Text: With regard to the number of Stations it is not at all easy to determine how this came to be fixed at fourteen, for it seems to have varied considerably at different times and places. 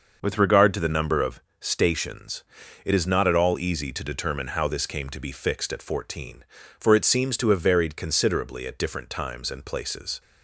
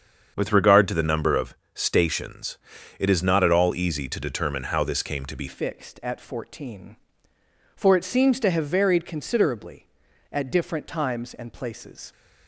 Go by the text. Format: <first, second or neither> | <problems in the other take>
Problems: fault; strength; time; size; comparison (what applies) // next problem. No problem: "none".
first | starts louder than the rest; until 1.3 s; 7 dB // pauses between "of" and "Stations"; slight; at 1.5 s; 0.22 s long; slight in the first // pauses between "Stations" and "it"; at 2.5 s; 0.44 s long; also in the first // changes voice at "fixed"; from 5.4 s on; 6.7 s long